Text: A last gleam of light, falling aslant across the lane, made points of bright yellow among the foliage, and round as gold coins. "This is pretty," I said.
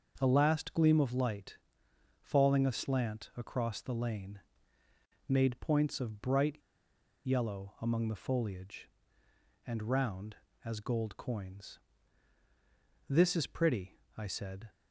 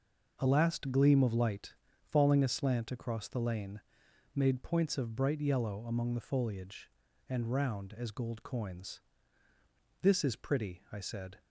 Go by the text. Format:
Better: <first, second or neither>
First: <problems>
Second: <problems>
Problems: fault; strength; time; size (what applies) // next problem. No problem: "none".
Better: second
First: starts louder than the rest; until 1.1 s; 6 dB // pauses between "bright" and "yellow"; noticeable; at 6.5 s; 0.68 s long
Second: none